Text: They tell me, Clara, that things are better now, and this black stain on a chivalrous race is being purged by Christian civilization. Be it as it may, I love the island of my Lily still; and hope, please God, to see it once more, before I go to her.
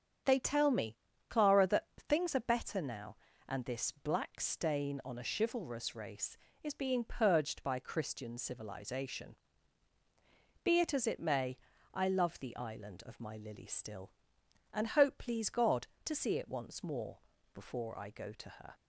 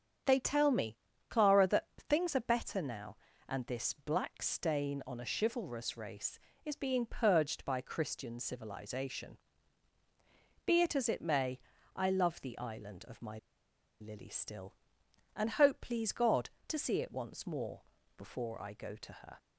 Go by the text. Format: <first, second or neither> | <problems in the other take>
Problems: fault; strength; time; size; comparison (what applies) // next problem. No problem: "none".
first | starts louder than the rest; strong; until 1.5 s; 8 dB; strong in the first // pauses between "my" and "Lily"; noticeable; at 13.3 s; 0.63 s long